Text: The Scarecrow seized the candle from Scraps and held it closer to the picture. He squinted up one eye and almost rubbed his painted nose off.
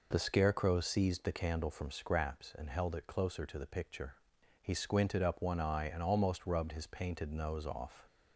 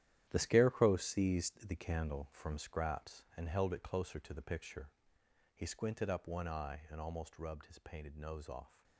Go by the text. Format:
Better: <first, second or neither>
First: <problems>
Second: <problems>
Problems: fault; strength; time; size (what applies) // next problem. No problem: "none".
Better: first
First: none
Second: gets quieter; strong; throughout; 11 dB